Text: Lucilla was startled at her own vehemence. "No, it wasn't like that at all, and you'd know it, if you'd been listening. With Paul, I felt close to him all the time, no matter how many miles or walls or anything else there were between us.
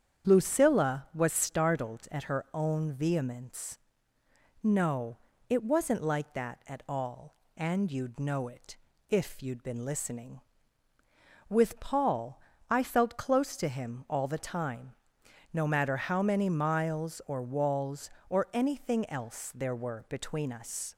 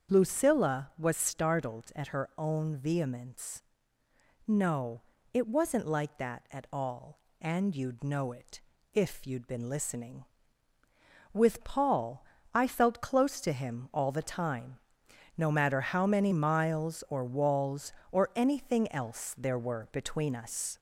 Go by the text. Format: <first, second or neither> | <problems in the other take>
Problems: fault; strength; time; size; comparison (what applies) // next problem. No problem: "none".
first | gets louder; slight; throughout; 2 dB // starts louder than the rest; strong; until 1.2 s; 7.5 dB; strong in the first